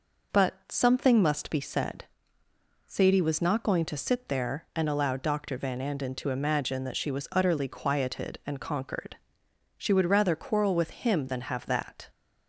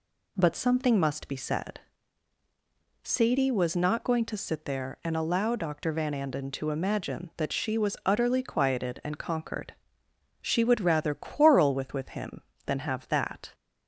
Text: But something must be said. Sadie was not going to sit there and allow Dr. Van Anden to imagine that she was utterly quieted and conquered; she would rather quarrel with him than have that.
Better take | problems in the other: first | says "with" twice; at 11.9 s

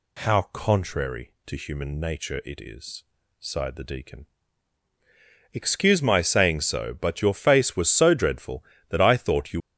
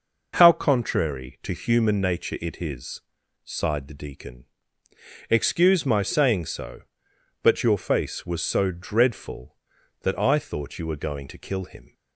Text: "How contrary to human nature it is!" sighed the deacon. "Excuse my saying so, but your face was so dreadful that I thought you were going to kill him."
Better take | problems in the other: second | stops before "were going to kill him"; at 9.6 s

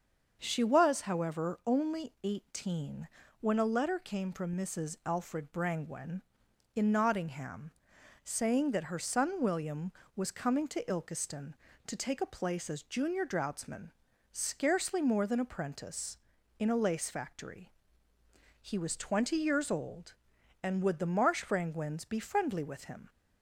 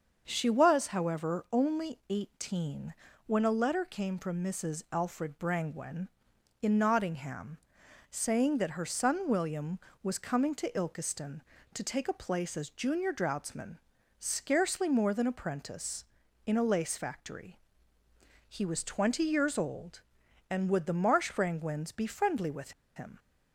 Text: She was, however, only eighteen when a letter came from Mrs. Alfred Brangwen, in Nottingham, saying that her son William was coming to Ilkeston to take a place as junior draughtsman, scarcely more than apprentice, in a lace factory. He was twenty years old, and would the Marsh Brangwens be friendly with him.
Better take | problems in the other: first | starts louder than the rest; until 1.2 s; 6.5 dB; also in the first // pauses between "eighteen" and "when"; slight; at 2.9 s; 0.34 s long; slight in the first // pauses between "with" and "him"; slight; at 22.7 s; 0.24 s long

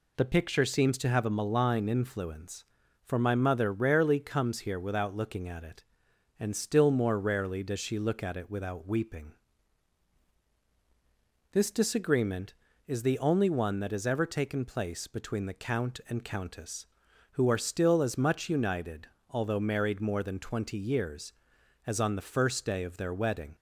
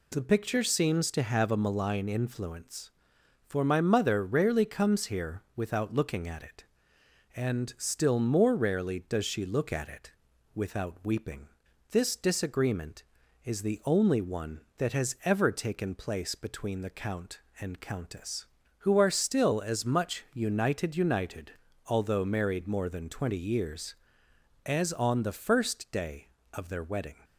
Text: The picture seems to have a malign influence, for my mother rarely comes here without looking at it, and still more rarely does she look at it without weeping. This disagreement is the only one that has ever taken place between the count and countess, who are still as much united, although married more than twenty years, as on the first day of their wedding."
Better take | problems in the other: first | pauses between "here" and "without"; slight; at 5.4 s; 0.16 s long // pauses between "it" and "without"; at 10.1 s; 0.42 s long // says "united" twice; at 20.9 s

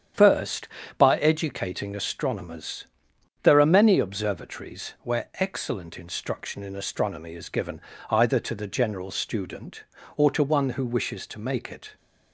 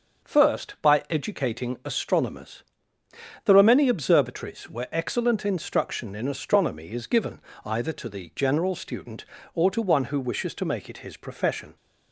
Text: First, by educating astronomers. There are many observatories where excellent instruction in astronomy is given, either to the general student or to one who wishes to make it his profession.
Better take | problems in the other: second | starts louder than the rest; strong; until 1.4 s; 9 dB; also in the second // stops before "his profession"; at 11.9 s

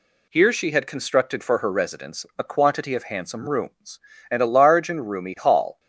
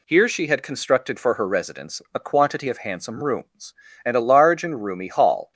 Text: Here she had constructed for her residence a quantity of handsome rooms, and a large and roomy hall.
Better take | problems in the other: neither | none

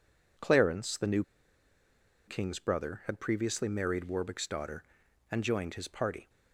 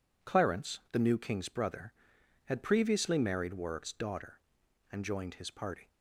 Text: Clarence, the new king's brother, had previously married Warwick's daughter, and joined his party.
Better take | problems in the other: second | pauses between "new" and "king's"; at 1.2 s; 1.0 s long

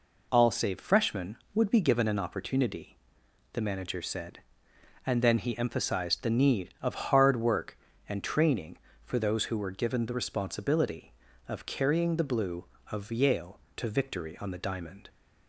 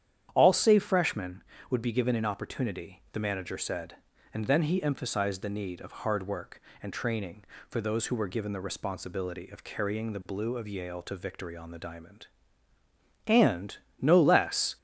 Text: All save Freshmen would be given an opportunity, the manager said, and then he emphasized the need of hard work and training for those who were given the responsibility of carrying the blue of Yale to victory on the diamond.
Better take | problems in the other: first | starts louder than the rest; strong; until 1.3 s; 9.5 dB // goes on to say "And no less"; from 13.2 s on; 1.5 s long

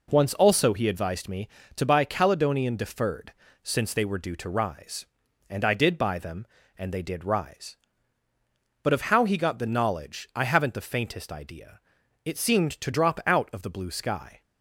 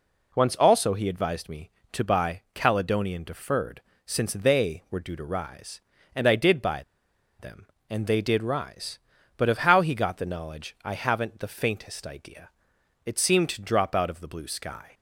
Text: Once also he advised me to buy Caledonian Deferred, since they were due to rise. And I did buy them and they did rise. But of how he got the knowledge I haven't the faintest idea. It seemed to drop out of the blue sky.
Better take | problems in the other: first | pauses between "buy" and "them"; noticeable; at 6.8 s; 0.57 s long

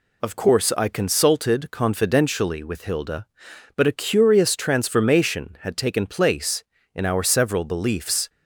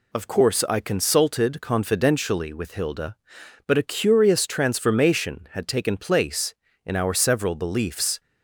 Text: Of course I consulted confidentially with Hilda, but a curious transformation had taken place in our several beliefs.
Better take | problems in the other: neither | none

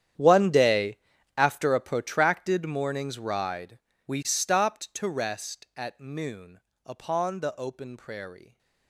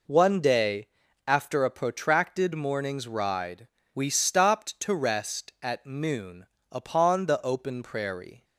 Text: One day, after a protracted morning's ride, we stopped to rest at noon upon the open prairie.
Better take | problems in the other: second | gets quieter; strong; throughout; 19 dB // pauses between "noon" and "upon"; slight; at 6.5 s; 0.24 s long; slight in the second

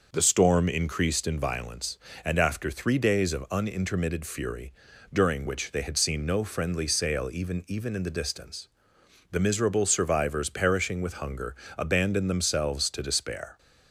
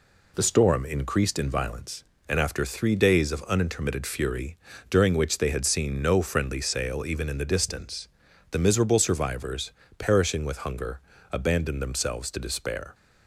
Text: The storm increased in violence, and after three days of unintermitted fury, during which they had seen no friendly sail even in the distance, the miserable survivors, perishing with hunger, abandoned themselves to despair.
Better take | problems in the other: second | says "even" twice; at 7.6 s

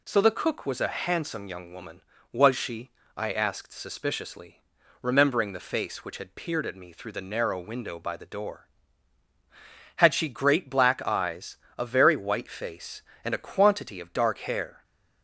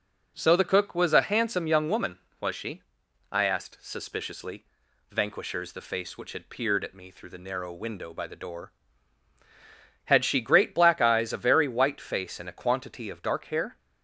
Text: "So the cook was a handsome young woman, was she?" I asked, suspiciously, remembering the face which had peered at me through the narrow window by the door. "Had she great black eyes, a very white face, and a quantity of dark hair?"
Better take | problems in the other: first | says "vanquishers" for "remembering"; at 5.0 s

